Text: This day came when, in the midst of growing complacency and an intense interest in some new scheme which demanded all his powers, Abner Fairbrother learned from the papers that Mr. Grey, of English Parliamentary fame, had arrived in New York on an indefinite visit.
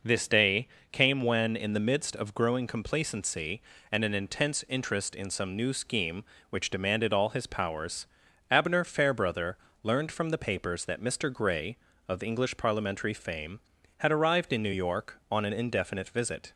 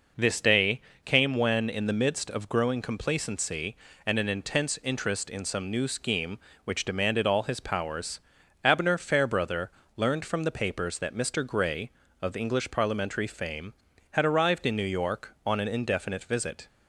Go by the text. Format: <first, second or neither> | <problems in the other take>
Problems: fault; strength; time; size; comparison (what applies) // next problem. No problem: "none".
neither | pauses between "day" and "came"; slight; the same in both // pauses between "Fairbrother" and "learned"; slight; the same in both